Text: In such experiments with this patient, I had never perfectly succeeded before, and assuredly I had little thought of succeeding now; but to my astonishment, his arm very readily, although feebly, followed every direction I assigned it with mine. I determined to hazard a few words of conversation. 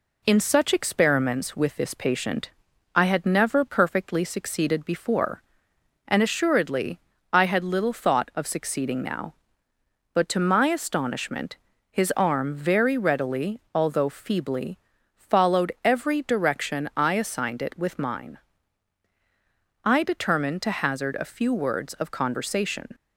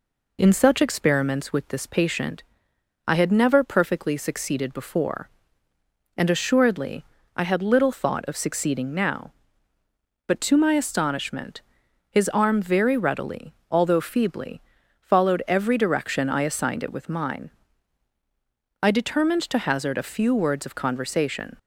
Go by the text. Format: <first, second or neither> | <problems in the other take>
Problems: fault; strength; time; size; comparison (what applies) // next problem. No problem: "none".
neither | pauses between "assuredly" and "I"; slight; the same in both